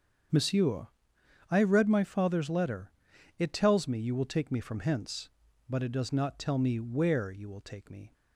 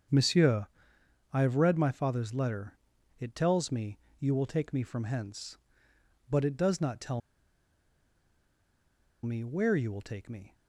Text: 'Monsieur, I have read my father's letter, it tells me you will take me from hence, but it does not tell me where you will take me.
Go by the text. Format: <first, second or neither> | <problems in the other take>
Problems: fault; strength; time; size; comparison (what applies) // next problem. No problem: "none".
first | starts louder than the rest; strong; until 1.7 s; 7.5 dB; strong in the first // pauses between "me" and "you"; slight; at 3.9 s; 0.20 s long // pauses between "tell" and "me"; strong; at 7.2 s; 2.0 s long